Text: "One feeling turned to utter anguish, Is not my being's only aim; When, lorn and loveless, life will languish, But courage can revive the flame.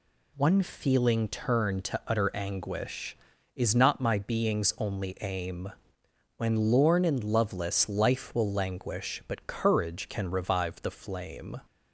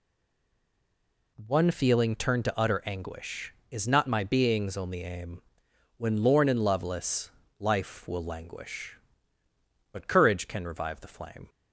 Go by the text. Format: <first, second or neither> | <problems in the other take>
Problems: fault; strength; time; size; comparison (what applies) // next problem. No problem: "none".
first | stays silent before the first word; noticeable; until 1.3 s; 1.3 s long